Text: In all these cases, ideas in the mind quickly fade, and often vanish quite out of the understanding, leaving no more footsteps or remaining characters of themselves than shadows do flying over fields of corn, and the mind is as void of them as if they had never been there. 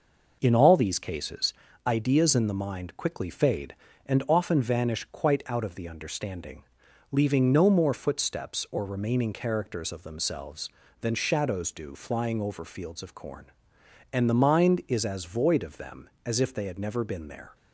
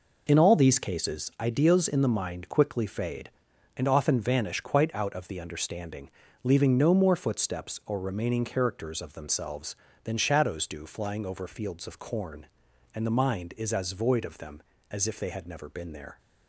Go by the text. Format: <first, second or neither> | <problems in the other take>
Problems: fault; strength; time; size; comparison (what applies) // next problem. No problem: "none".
neither | none